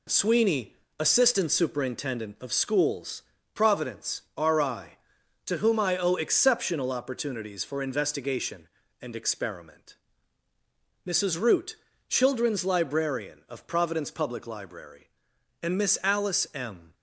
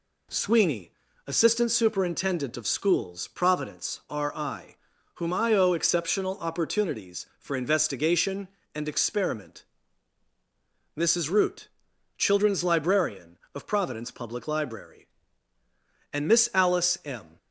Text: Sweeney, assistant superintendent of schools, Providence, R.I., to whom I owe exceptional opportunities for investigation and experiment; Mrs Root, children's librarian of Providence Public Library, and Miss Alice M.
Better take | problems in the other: first | skips "to"; at 4.9 s

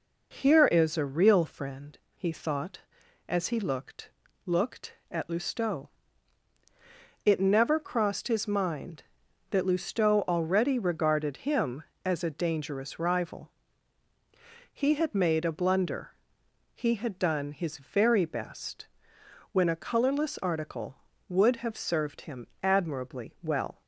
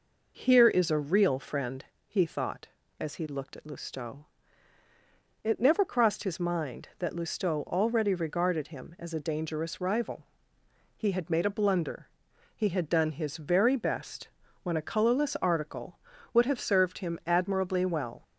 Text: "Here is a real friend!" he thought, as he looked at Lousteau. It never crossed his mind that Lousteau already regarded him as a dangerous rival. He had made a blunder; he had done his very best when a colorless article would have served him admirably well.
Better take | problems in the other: second | says "looked" twice; at 4.4 s // pauses between "best" and "when"; noticeable; at 18.8 s; 0.66 s long; slight in the second // pauses between "him" and "admirably"; slight; at 22.4 s; 0.16 s long

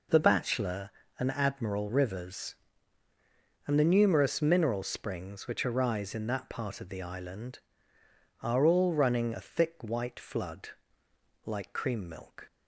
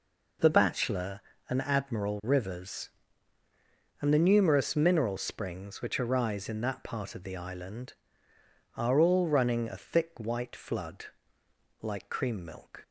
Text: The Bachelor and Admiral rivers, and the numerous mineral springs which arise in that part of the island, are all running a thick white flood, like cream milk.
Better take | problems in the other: neither | none

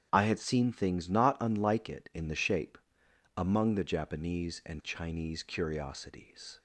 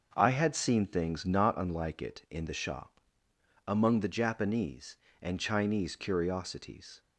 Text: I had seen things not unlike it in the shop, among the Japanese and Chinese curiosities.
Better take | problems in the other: second | starts louder than the rest; strong; until 1.1 s; 9 dB; noticeable in the second // says "shape" for "shop"; at 2.3 s

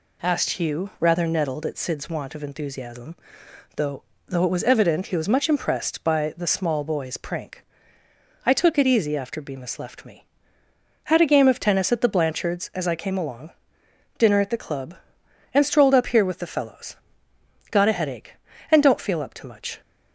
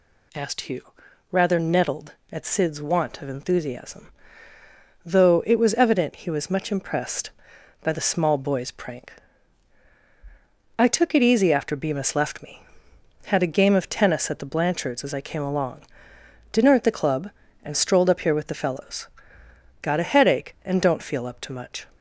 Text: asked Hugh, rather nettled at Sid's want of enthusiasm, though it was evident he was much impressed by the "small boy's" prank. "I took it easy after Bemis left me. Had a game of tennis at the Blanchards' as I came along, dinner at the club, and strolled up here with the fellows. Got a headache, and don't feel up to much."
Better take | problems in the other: second | says "though" twice; at 4.2 s

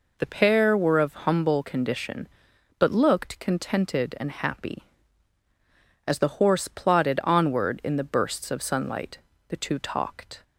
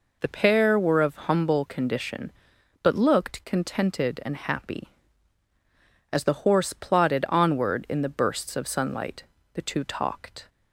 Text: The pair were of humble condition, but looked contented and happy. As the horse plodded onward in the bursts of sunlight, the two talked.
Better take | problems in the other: neither | none

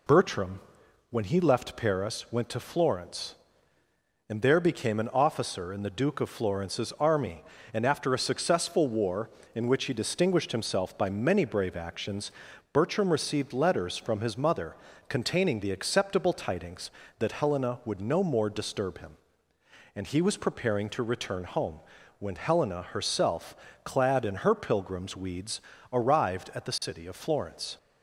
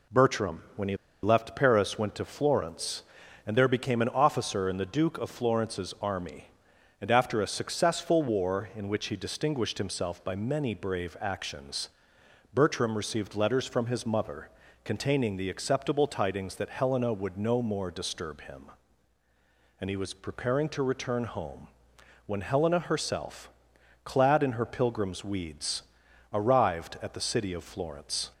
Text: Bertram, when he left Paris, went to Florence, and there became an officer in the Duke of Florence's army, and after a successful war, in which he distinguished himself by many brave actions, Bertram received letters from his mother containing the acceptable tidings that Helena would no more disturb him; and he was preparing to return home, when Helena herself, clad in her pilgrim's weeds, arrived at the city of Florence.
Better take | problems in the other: first | pauses between "he" and "left"; slight; at 0.9 s; 0.27 s long // pauses between "mother" and "containing"; slight; at 14.4 s; 0.34 s long; slight in the first

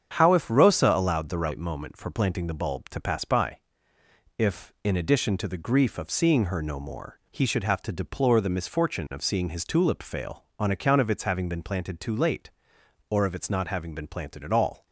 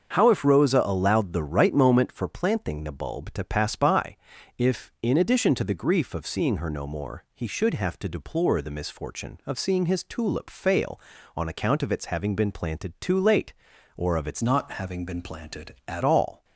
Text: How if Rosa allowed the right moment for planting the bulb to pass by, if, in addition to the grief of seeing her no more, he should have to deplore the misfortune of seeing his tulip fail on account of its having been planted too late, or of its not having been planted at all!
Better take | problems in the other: first | starts louder than the rest; until 1.1 s; 7 dB; strong in the first // changes voice from "not" to "at"; from 14.4 to 16.0 s; 1.6 s long

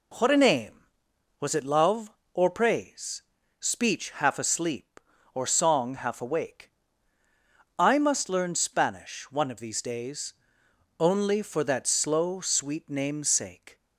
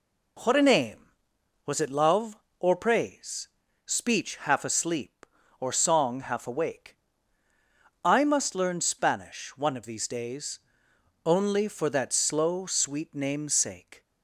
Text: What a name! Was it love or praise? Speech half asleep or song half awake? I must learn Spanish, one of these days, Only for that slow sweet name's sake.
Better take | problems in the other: neither | none

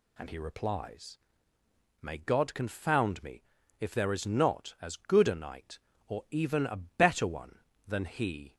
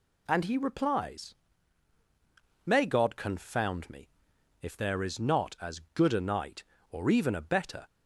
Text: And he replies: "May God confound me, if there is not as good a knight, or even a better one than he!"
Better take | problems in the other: first | stops before "one than he"; at 7.8 s

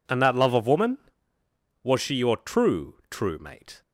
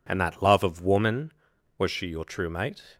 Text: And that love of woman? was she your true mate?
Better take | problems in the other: second | says "true" twice; at 3.1 s

